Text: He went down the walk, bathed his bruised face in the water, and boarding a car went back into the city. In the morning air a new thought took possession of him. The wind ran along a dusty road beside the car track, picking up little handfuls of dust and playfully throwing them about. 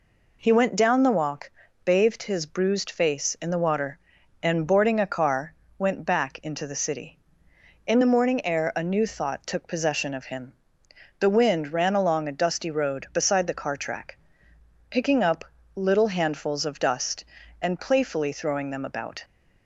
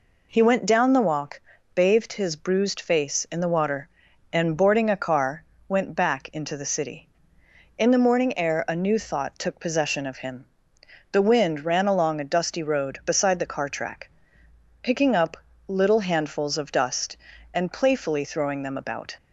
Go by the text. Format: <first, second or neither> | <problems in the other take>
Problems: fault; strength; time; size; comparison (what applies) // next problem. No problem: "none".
neither | pauses between "car" and "went"; slight; the same in both // pauses between "up" and "little"; slight; the same in both